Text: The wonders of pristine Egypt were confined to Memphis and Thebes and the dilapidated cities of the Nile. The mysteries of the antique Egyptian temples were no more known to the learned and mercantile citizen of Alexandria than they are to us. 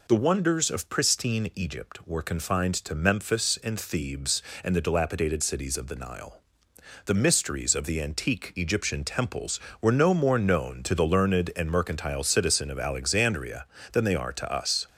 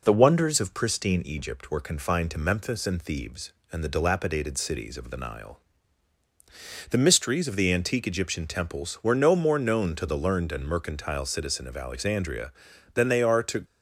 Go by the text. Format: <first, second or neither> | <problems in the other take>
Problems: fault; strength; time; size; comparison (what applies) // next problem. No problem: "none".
first | stops before "us"; at 13.6 s